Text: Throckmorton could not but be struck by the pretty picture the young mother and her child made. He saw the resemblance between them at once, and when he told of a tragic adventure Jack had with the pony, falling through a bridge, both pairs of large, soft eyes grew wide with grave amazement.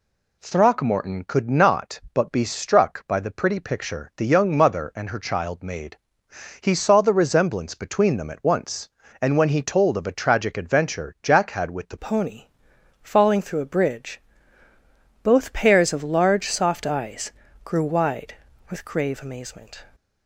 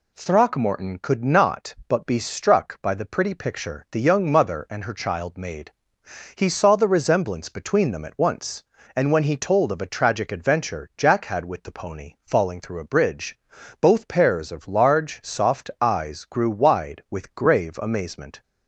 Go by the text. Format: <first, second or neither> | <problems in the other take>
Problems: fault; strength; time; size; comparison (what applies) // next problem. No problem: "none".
second | changes voice at "pony"; from 11.9 s on; 7.9 s long // pauses between "eyes" and "grew"; slight; at 17.3 s; 0.32 s long